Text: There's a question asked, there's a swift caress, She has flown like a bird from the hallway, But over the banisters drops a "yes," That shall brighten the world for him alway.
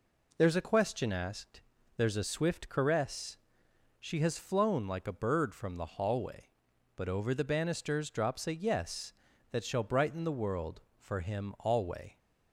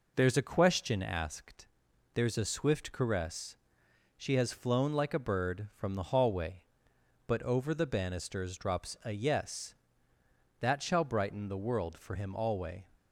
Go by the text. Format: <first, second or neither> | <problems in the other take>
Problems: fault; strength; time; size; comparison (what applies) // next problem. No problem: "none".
neither | none